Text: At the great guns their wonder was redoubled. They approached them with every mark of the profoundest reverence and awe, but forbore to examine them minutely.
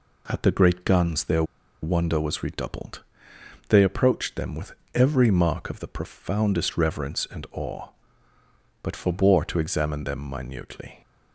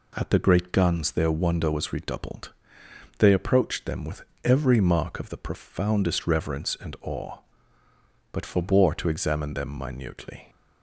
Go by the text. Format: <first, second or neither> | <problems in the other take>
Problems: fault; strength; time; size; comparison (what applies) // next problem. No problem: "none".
second | pauses between "their" and "wonder"; at 1.4 s; 0.38 s long // pauses between "with" and "every"; slight; at 4.7 s; 0.22 s long; slight in the second